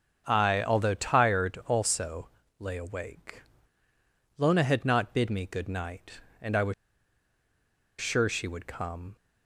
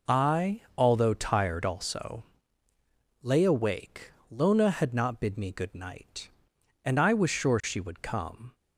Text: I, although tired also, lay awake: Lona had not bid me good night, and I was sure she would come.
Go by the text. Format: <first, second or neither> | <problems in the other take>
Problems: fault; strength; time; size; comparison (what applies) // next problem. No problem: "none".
second | starts louder than the rest; until 1.2 s; 7 dB // pauses between "was" and "sure"; strong; at 6.7 s; 1.2 s long